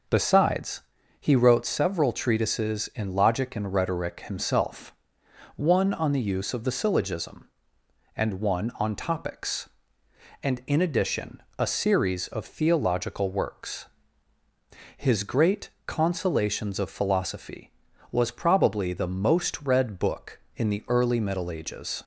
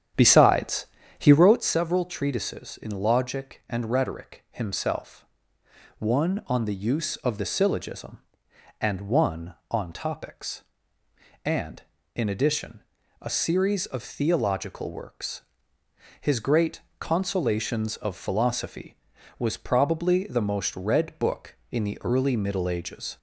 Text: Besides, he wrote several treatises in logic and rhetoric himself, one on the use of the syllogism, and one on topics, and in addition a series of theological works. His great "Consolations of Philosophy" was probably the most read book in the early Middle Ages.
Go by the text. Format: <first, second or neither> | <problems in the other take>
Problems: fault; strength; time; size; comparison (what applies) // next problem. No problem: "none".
first | starts louder than the rest; strong; until 1.6 s; 9.5 dB // pauses between "addition" and "a"; at 12.8 s; 0.40 s long; slight in the first // pauses between "great" and "Consolations"; slight; at 16.8 s; 0.18 s long; slight in the first